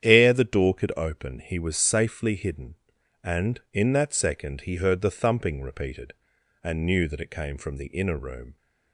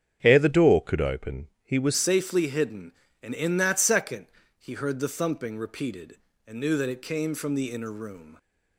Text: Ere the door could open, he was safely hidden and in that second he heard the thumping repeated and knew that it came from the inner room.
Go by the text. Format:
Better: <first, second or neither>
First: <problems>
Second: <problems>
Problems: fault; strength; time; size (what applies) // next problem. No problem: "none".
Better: first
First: starts louder than the rest; strong; until 1.0 s; 9.5 dB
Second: starts louder than the rest; strong; until 1.2 s; 8.5 dB // changes voice at "safely"; from 1.9 s on; 6.4 s long // pauses between "second" and "he"; slight; at 4.2 s; 0.30 s long